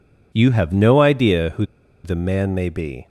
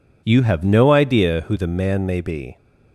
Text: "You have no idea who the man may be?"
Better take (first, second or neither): second